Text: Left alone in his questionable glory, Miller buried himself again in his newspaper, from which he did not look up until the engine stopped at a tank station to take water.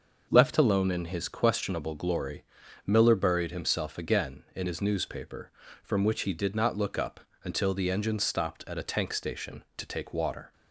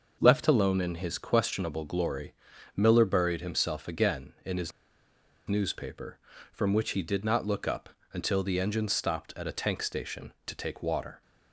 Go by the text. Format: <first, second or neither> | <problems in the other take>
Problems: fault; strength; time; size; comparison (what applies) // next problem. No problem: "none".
first | starts louder than the rest; noticeable; until 1.2 s; 6 dB; noticeable in the first // pauses between "his" and "newspaper"; noticeable; at 4.7 s; 0.78 s long // pauses between "up" and "until"; slight; at 7.8 s; 0.24 s long; slight in the first